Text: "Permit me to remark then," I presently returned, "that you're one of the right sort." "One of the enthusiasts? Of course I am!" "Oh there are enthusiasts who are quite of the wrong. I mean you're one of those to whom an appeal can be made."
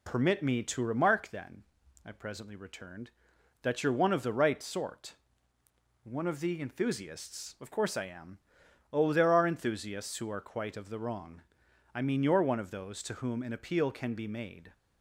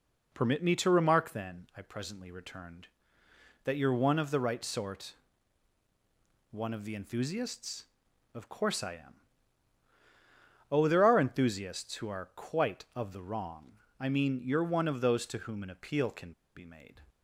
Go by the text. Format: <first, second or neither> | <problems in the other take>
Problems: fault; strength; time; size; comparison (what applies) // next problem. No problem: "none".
first | pauses between "can" and "be"; slight; at 16.3 s; 0.23 s long